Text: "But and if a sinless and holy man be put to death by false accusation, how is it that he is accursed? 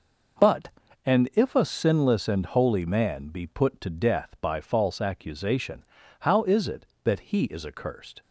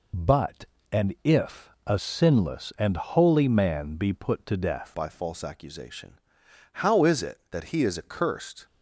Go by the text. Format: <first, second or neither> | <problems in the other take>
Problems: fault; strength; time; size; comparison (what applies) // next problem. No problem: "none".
first | changes voice at "by"; from 4.9 s on; 3.7 s long